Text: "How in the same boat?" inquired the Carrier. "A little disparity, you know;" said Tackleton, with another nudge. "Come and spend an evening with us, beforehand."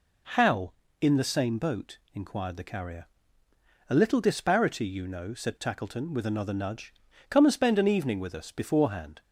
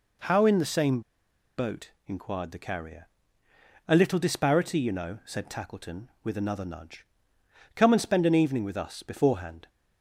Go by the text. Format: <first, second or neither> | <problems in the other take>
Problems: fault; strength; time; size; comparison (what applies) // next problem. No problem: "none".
first | pauses between "same" and "boat"; noticeable; at 0.9 s; 0.57 s long